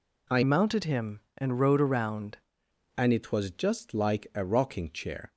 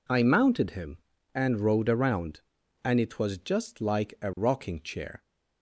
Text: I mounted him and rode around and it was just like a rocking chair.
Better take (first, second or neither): second